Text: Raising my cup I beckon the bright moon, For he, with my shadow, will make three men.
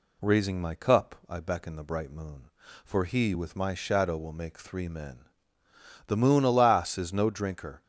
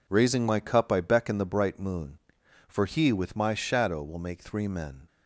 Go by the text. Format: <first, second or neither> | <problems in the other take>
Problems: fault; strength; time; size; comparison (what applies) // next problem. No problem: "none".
second | goes on to say "The moon alas is no drinker"; strong; from 6.0 s on; 1.7 s long